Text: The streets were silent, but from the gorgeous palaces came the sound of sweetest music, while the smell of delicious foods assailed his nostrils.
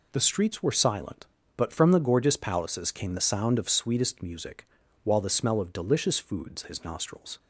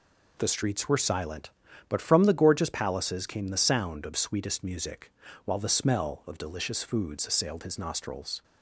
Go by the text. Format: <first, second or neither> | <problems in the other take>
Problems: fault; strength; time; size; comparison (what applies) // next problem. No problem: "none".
second | skips "assailed"; at 6.6 s